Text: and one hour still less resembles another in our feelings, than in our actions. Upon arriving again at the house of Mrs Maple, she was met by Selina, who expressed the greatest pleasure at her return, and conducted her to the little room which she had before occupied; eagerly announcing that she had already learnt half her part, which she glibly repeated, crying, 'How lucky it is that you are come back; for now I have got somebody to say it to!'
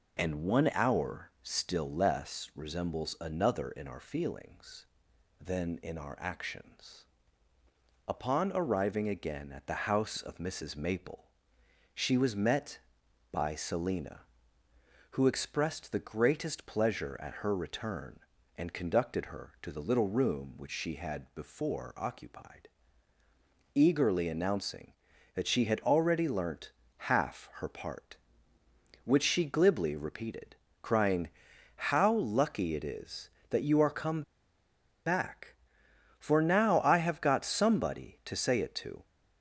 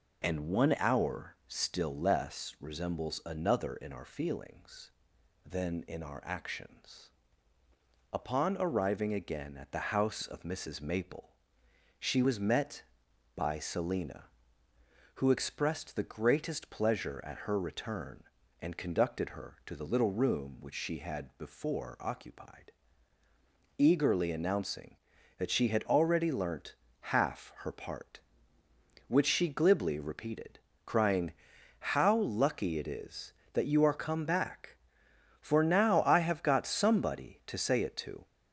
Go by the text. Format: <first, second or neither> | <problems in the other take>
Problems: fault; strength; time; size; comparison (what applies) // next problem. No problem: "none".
second | pauses between "learnt" and "half"; slight; at 26.7 s; 0.30 s long; slight in the second // pauses between "come" and "back"; noticeable; at 34.2 s; 0.84 s long